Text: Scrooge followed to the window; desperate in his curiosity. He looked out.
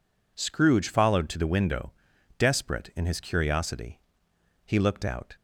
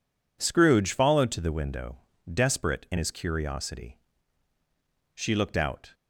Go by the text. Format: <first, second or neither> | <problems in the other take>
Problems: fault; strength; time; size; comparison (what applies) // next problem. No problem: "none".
first | says "She" for "He"; at 5.1 s